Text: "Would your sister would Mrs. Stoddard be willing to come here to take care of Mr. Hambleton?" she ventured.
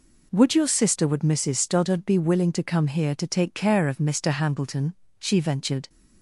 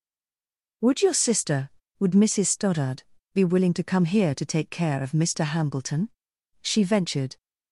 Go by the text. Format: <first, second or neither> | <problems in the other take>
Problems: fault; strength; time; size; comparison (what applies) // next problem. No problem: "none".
first | stays silent before the first word; slight; until 0.8 s; 0.8 s long // pauses between "Stoddard" and "be"; slight; at 3.0 s; 0.30 s long